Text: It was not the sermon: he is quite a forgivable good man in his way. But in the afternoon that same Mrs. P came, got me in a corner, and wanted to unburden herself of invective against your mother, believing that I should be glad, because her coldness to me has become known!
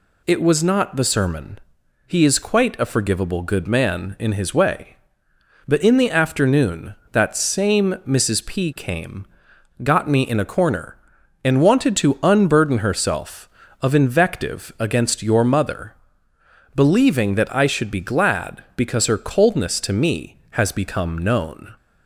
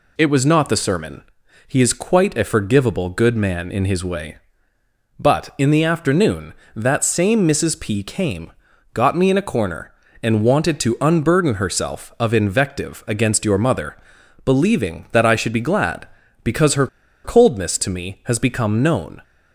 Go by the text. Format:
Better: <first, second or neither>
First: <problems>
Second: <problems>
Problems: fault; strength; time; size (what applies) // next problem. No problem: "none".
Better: first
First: none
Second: pauses between "her" and "coldness"; at 16.8 s; 0.36 s long